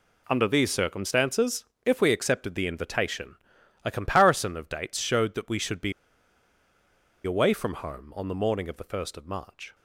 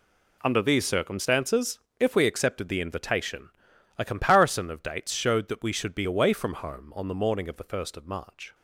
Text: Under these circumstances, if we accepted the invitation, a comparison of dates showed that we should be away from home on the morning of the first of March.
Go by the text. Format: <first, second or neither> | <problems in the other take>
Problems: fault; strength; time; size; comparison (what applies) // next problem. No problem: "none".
second | pauses between "be" and "away"; strong; at 5.9 s; 1.3 s long